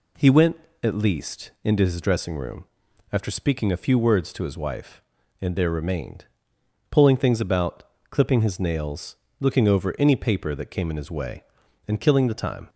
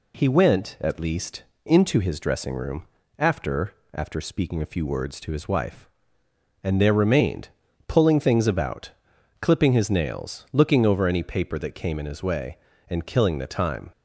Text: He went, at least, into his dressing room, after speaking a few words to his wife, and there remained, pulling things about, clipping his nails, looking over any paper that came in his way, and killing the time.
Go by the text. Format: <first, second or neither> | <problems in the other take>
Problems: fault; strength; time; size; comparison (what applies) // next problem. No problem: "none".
first | says "after" twice; at 3.9 s